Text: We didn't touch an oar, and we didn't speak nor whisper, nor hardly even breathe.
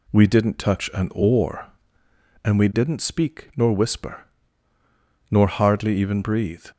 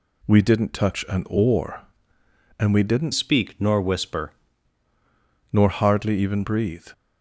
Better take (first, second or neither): first